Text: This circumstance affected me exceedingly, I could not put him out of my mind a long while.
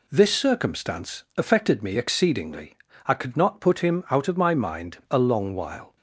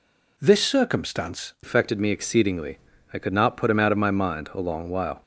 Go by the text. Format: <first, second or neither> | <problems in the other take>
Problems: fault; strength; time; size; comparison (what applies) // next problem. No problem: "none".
first | changes voice at "affected"; from 1.6 s on; 3.6 s long